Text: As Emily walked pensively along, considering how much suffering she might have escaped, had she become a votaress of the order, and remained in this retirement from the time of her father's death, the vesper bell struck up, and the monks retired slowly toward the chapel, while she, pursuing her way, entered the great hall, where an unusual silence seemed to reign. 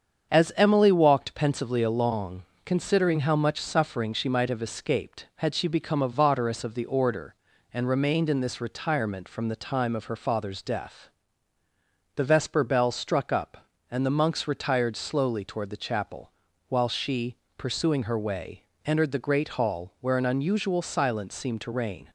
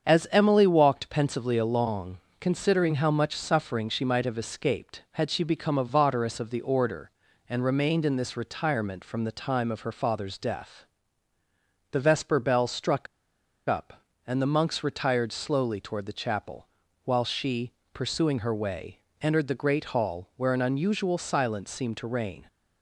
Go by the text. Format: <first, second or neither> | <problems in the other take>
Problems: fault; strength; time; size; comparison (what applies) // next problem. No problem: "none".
first | starts louder than the rest; strong; until 1.1 s; 7 dB; strong in the first // pauses between "struck" and "up"; noticeable; at 13.0 s; 0.61 s long